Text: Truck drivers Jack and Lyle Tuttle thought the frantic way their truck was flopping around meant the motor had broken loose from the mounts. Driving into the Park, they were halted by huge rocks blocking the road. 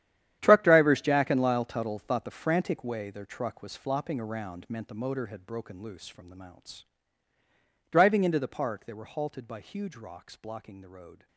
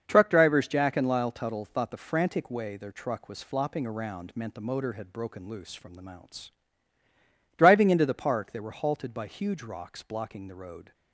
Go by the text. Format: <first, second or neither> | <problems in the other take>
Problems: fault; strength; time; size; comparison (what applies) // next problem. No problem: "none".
second | gets quieter; strong; throughout; 15.5 dB // starts louder than the rest; strong; until 1.4 s; 10.5 dB; also in the second